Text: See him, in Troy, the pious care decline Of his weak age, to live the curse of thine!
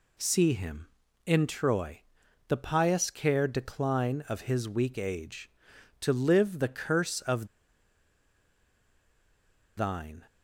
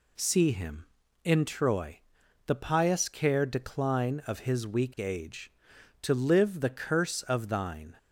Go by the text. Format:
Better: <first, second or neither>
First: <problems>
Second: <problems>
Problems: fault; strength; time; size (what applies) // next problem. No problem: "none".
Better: second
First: pauses between "of" and "thine"; strong; at 7.4 s; 2.3 s long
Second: none